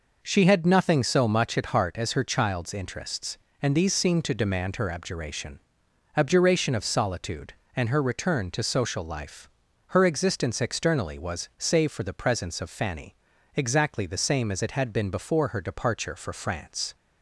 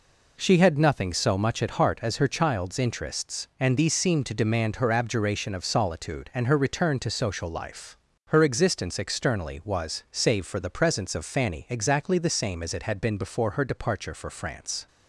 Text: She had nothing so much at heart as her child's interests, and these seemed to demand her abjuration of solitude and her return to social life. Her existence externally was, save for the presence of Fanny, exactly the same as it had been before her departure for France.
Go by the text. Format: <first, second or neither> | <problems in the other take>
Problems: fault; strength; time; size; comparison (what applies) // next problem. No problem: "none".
second | says "abjuration" twice; at 6.1 s